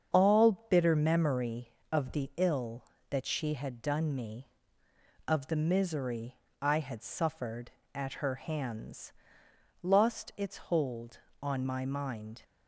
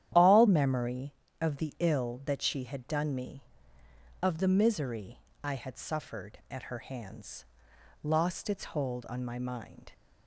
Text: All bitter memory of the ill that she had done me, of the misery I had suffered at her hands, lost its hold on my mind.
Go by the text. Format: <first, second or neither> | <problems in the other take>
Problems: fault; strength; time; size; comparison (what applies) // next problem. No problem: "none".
first | starts louder than the rest; strong; until 1.4 s; 11 dB; strong in the first // skips "bitter"; at 0.4 s // pauses between "misery" and "I"; slight; at 5.1 s; 0.24 s long; slight in the first